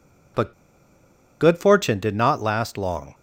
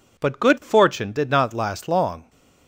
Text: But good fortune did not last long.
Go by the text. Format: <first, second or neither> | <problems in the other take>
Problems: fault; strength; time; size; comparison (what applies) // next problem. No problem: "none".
second | pauses between "But" and "good"; noticeable; at 0.5 s; 0.89 s long